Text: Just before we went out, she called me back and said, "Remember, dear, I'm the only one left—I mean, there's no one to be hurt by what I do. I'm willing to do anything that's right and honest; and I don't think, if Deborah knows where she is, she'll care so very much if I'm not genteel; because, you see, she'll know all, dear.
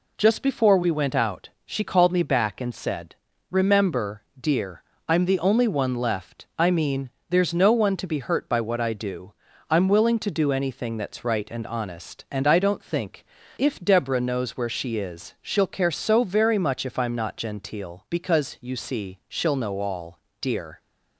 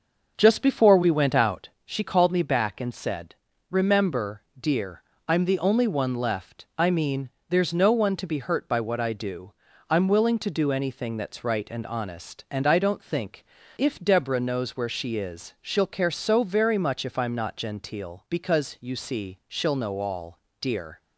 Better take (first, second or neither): first